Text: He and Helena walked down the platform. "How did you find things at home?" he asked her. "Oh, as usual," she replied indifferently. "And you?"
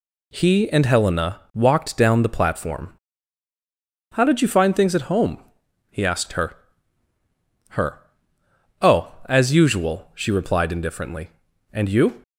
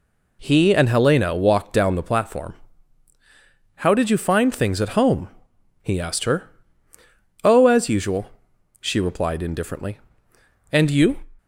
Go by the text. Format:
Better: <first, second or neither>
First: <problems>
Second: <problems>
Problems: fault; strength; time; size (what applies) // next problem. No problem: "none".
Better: second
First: says "her" twice; at 7.7 s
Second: none